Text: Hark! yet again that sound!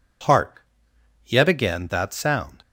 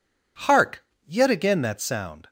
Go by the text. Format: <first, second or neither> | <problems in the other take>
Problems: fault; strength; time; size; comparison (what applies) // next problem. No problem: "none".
neither | none